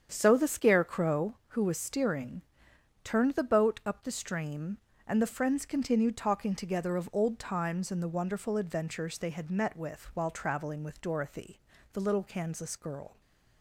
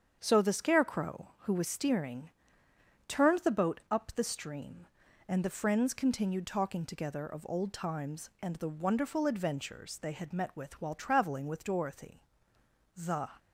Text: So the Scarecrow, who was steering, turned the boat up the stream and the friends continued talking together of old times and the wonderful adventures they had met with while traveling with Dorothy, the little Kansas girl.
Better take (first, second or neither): first